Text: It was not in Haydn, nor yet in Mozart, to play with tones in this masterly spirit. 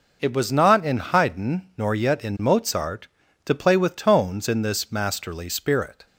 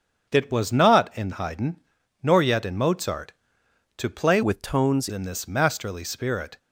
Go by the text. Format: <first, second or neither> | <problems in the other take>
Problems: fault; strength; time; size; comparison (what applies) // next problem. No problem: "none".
first | starts louder than the rest; until 1.3 s; 7 dB // changes voice from "with" to "tones"; from 4.4 to 5.0 s; 0.6 s long